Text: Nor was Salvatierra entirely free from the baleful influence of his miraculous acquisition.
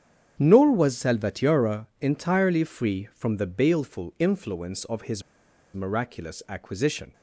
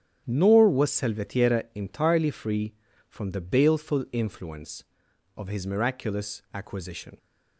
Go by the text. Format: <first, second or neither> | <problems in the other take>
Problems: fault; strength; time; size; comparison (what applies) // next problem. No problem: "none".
second | starts louder than the rest; strong; until 1.3 s; 8.5 dB; strong in the second // pauses between "his" and "miraculous"; noticeable; at 5.2 s; 0.52 s long